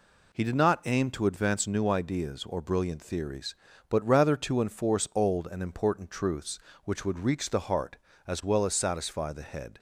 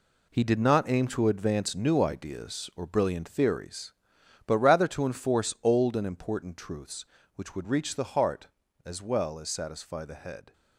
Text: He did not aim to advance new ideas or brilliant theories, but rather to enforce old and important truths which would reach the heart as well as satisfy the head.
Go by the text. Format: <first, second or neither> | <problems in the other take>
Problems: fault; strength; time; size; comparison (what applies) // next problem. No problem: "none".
first | gets quieter; strong; throughout; 9 dB